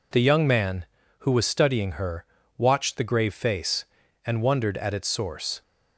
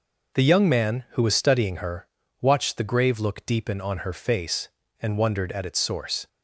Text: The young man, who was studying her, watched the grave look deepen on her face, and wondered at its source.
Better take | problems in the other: second | skips "look deepen on her"; at 3.3 s

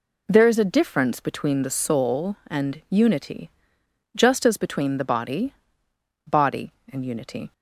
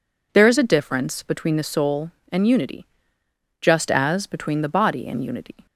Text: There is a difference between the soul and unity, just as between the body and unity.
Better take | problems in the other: second | says "body" twice; at 6.2 s

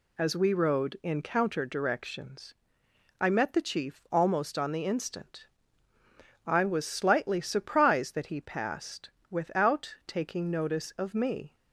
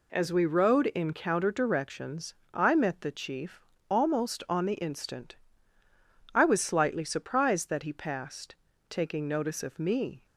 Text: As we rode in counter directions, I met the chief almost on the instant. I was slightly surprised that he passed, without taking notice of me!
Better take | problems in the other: first | pauses between "chief" and "almost"; slight; at 3.6 s; 0.28 s long // skips "without"; at 8.7 s

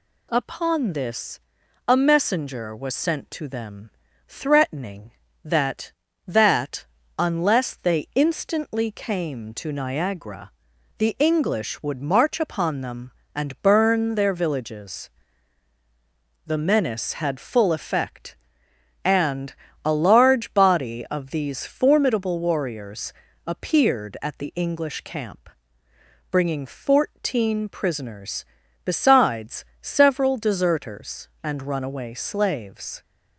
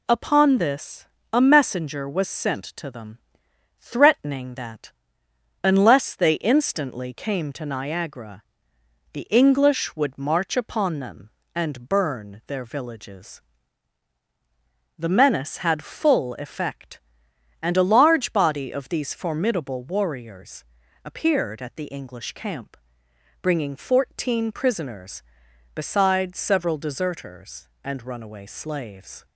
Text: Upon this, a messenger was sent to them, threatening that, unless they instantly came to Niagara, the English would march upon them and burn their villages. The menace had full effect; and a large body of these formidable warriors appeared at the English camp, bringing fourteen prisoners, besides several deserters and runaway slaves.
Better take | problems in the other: second | says "that" twice; at 6.2 s // pauses between "and" and "a"; slight; at 19.5 s; 0.30 s long // pauses between "warriors" and "appeared"; slight; at 23.1 s; 0.36 s long; also in the second // pauses between "besides" and "several"; slight; at 29.6 s; 0.18 s long

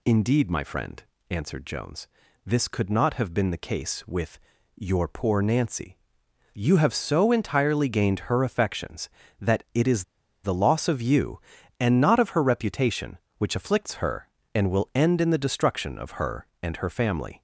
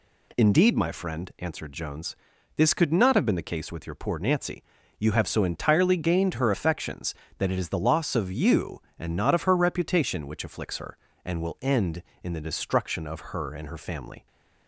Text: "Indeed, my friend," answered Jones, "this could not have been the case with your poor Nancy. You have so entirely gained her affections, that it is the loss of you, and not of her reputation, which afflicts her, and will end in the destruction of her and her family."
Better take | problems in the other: second | pauses between "with" and "your"; slight; at 4.4 s; 0.34 s long // pauses between "is" and "the"; at 10.0 s; 0.39 s long

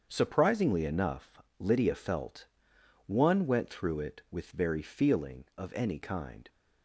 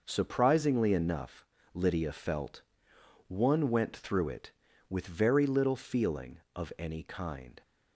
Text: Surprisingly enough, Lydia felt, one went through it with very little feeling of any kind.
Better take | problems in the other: second | starts louder than the rest; strong; until 1.1 s; 7.5 dB // skips "little"; at 4.8 s

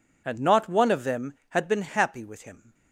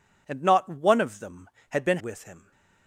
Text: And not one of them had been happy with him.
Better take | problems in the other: first | skips "happy"; at 1.9 s

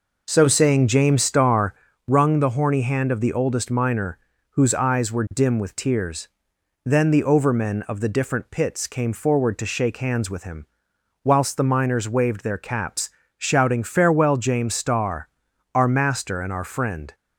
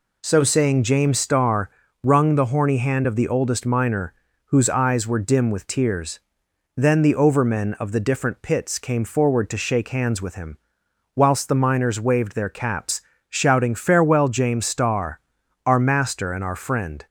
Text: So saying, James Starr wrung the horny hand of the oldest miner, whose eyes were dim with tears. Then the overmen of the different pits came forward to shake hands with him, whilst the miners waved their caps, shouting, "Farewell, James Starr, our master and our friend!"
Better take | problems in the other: second | starts louder than the rest; noticeable; until 2.1 s; 5 dB // pauses between "Starr" and "wrung"; slight; at 1.7 s; 0.32 s long; slight in the second

